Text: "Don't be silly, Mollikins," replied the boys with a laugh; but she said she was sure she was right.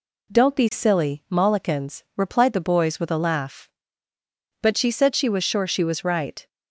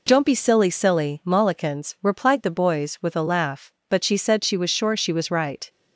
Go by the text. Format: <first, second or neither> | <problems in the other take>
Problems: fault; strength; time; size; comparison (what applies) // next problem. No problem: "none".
first | says "silly" twice; at 0.6 s